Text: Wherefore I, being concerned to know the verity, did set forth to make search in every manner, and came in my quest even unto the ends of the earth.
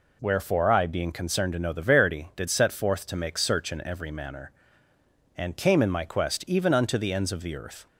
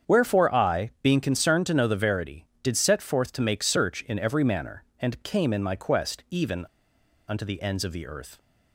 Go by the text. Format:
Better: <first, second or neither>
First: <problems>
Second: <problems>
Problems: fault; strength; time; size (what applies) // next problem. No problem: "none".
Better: first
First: none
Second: starts louder than the rest; strong; until 1.1 s; 7.5 dB // pauses between "even" and "unto"; noticeable; at 6.6 s; 0.63 s long